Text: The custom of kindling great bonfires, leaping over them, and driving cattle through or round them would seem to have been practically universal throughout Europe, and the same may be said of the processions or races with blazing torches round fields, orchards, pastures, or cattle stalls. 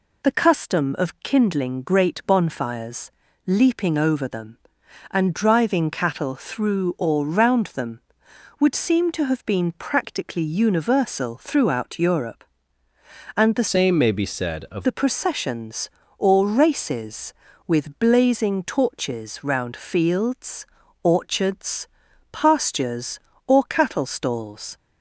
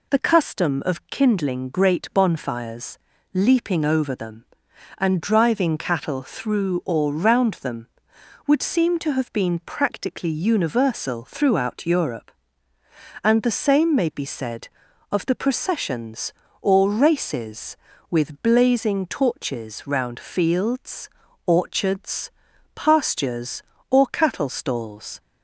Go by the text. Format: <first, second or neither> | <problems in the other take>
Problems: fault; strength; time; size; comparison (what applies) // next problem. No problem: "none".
second | changes voice from "same" to "of"; from 13.6 to 14.8 s; 1.2 s long